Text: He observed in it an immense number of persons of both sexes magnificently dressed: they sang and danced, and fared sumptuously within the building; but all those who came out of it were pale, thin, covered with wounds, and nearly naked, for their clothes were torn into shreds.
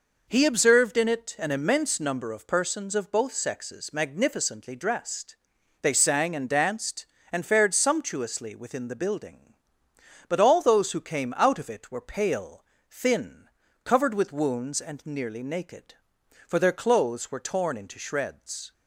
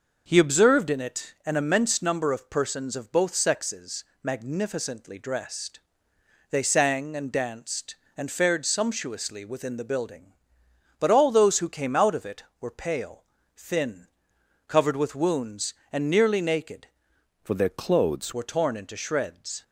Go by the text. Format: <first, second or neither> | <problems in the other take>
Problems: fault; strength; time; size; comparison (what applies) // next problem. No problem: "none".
first | pauses between "sexes" and "magnificently"; slight; at 4.0 s; 0.22 s long // changes voice from "for" to "clothes"; from 17.4 to 18.3 s; 0.9 s long